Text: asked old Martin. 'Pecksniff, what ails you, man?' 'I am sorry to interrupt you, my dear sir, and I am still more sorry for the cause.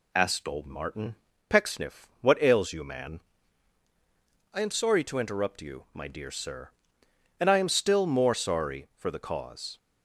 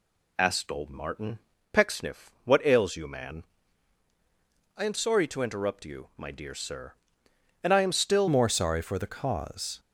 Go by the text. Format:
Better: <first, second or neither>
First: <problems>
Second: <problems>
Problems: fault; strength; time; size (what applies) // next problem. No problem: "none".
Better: first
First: none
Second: changes voice at "more"; from 8.2 s on; 1.5 s long